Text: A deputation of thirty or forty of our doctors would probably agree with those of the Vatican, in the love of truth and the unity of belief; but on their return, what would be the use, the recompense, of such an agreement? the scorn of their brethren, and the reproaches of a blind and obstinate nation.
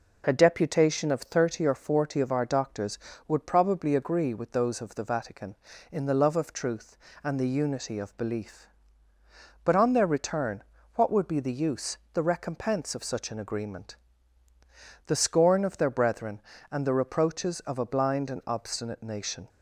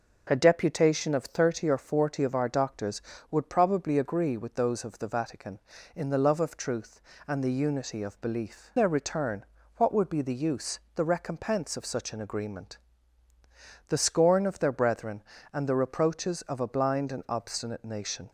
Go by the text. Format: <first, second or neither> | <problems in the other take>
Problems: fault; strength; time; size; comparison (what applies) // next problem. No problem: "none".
first | skips "but on"; at 8.7 s